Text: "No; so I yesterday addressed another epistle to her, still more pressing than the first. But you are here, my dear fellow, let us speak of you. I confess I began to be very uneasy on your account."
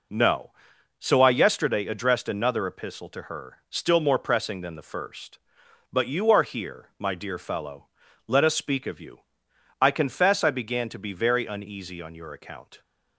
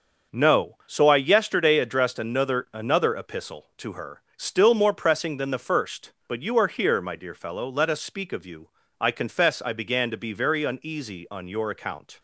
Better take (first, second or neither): first